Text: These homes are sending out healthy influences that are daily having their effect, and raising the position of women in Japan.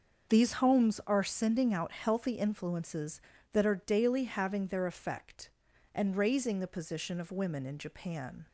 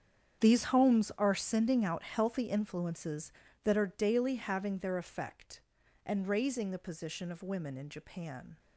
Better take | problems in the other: first | gets quieter; strong; throughout; 15 dB // starts louder than the rest; strong; until 1.4 s; 8 dB; noticeable in the first

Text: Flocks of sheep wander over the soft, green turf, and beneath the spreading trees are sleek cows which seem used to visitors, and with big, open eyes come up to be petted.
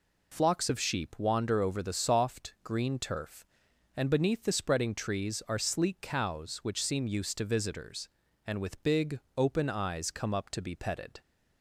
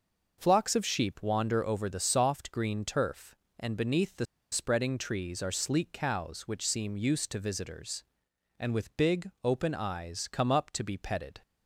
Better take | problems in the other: first | pauses between "the" and "spreading"; slight; at 4.2 s; 0.26 s long

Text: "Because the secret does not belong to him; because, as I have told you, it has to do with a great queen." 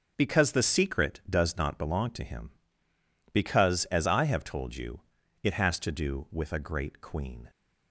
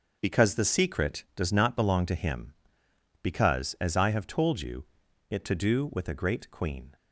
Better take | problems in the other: first | starts louder than the rest; until 1.2 s; 6.5 dB // skips "has"; at 5.4 s

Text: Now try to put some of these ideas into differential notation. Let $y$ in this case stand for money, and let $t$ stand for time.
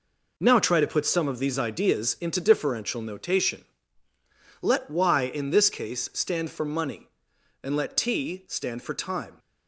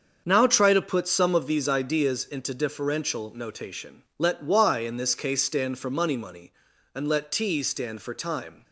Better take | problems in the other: first | starts louder than the rest; until 1.2 s; 7 dB // says "money" twice; at 6.1 s

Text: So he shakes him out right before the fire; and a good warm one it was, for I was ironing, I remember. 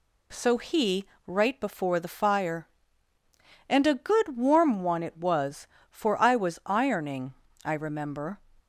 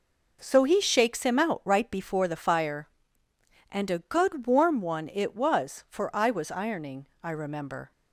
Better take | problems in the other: second | skips "shakes him out"; at 1.1 s

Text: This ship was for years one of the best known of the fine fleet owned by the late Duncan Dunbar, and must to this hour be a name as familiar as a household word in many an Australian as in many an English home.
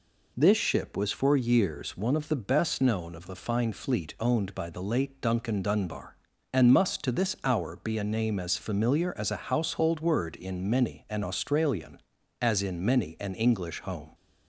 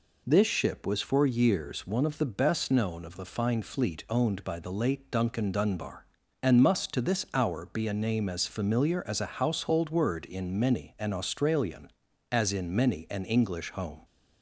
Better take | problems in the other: neither | none

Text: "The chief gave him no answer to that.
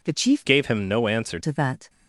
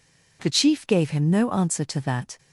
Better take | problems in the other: second | changes voice from "gave" to "answer"; from 0.4 to 1.3 s; 0.9 s long

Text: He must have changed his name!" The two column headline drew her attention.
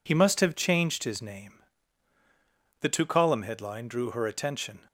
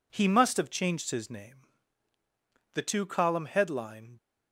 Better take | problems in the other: first | stops before "drew her attention"; at 4.1 s

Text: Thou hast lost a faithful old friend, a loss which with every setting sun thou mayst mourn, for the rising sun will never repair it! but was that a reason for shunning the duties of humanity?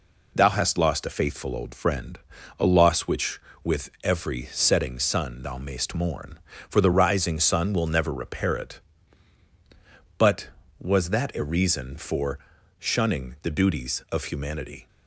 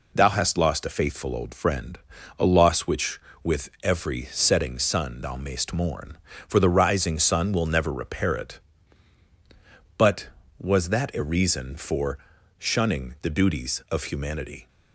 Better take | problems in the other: neither | pauses between "for" and "shunning"; the same in both

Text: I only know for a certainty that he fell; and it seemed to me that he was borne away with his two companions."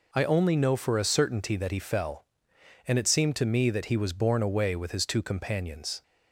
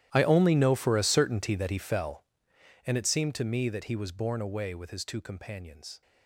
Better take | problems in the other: first | gets quieter; strong; throughout; 20.5 dB

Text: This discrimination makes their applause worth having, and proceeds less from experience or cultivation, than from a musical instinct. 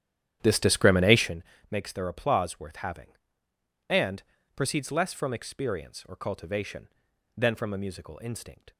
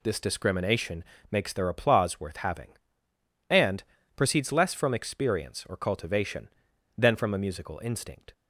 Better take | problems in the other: second | starts louder than the rest; strong; until 1.4 s; 10.5 dB // pauses between "discrimination" and "makes"; slight; at 1.4 s; 0.26 s long; slight in the second // pauses between "and" and "proceeds"; slight; at 4.2 s; 0.34 s long; slight in the second

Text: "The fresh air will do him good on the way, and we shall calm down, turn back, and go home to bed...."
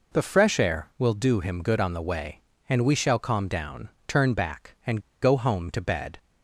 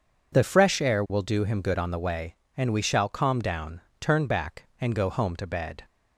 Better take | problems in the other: second | pauses between "and" and "go"; slight; at 5.0 s; 0.21 s long

